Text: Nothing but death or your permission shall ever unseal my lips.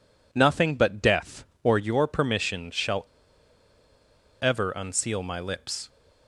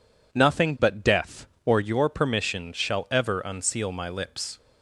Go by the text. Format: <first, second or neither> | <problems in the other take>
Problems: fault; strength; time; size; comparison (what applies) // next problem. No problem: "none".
second | pauses between "shall" and "ever"; strong; at 3.0 s; 1.3 s long